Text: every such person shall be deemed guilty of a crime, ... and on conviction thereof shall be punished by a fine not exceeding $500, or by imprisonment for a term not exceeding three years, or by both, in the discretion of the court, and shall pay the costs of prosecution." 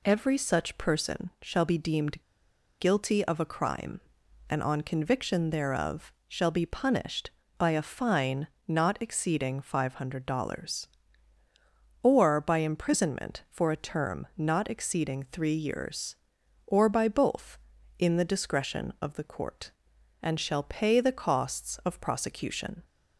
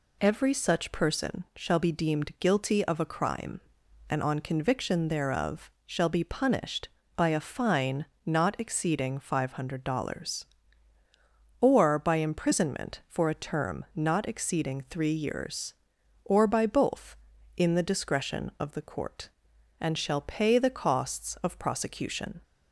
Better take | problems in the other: second | pauses between "deemed" and "guilty"; noticeable; at 2.1 s; 0.60 s long // pauses between "thereof" and "shall"; slight; at 6.1 s; 0.16 s long; slight in the second // pauses between "fine" and "not"; slight; at 8.4 s; 0.22 s long; slight in the second

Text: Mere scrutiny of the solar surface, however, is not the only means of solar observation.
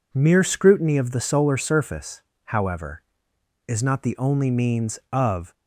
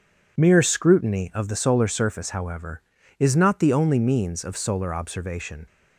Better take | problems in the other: second | stops before "solar observation"; at 5.5 s

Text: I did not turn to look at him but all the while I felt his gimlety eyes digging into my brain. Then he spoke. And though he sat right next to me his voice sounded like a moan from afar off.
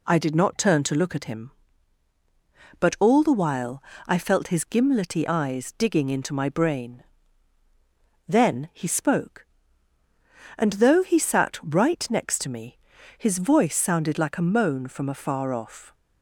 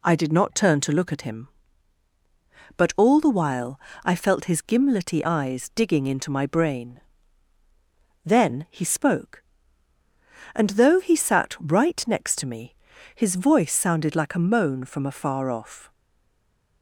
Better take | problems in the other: first | pauses between "while" and "I"; slight; at 3.7 s; 0.26 s long; slight in the first // pauses between "me" and "his"; at 12.7 s; 0.40 s long; also in the first // stays silent after the last word; slight; from 15.9 s on; 0.9 s long

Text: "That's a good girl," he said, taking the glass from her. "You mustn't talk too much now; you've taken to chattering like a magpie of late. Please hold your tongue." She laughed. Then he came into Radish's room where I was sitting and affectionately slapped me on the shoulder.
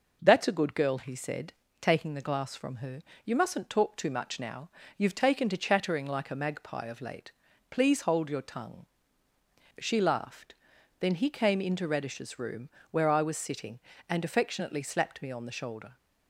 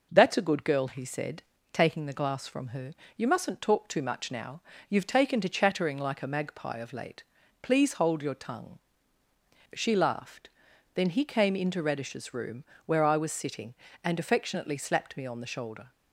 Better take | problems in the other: neither | pauses between "room" and "where"; slight; the same in both

